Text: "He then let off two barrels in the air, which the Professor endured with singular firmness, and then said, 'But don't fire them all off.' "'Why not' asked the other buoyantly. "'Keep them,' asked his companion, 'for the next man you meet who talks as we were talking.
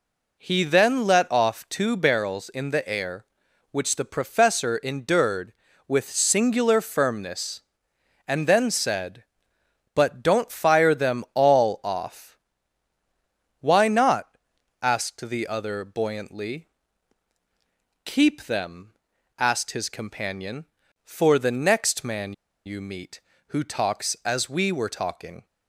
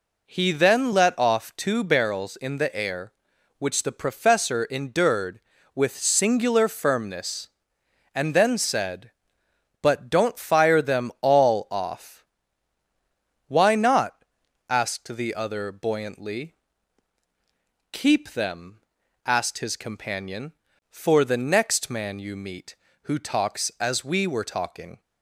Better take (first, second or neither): second